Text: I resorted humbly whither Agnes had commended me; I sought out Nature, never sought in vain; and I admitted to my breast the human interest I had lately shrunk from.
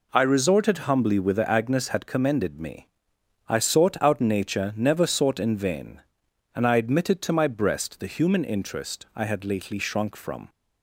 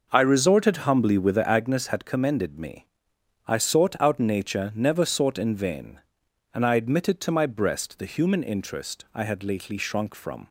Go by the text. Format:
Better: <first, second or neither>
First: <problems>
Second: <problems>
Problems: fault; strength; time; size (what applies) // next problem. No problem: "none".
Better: first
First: none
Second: starts louder than the rest; noticeable; until 1.7 s; 5.5 dB